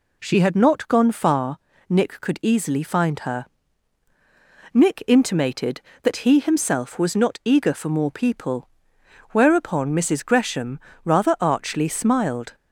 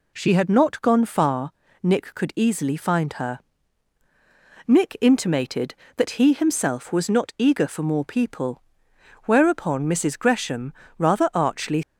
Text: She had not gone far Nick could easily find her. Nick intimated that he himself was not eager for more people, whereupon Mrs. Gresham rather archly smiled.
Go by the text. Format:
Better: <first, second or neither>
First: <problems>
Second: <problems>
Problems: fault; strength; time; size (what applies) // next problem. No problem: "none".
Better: first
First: pauses between "far" and "Nick"; slight; at 1.5 s; 0.32 s long // pauses between "Gresham" and "rather"; slight; at 10.7 s; 0.24 s long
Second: pauses between "far" and "Nick"; slight; at 1.5 s; 0.32 s long // pauses between "Gresham" and "rather"; slight; at 10.7 s; 0.24 s long // stops before "smiled"; at 11.8 s